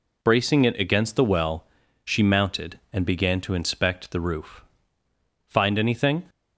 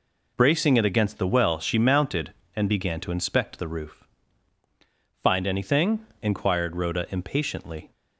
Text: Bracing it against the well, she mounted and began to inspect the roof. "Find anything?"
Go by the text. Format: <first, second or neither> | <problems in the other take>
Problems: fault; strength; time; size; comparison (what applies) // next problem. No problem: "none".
first | goes on to say "inquired Rhoda impatiently"; strong; from 6.2 s on; 1.6 s long